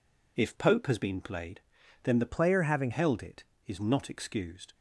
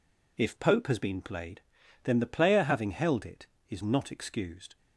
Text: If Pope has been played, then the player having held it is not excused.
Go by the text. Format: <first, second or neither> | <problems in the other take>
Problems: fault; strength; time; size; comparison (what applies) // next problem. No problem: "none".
second | changes voice from "player" to "having"; from 2.2 to 2.9 s; 0.7 s long